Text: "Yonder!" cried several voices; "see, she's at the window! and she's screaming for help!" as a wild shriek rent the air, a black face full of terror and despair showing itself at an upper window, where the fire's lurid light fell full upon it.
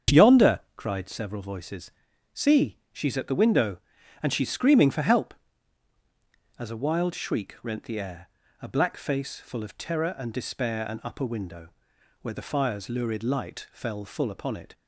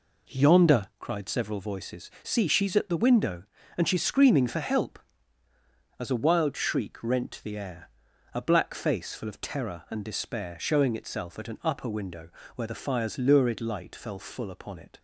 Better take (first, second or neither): second